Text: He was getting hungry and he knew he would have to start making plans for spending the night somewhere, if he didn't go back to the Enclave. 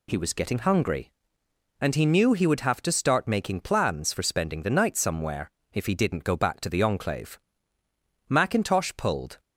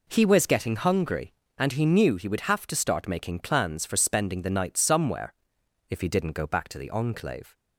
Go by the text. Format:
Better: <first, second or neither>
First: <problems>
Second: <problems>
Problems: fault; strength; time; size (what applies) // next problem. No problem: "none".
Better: second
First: goes on to say "MacIntosh pulled"; noticeable; from 8.2 s on; 1.1 s long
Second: none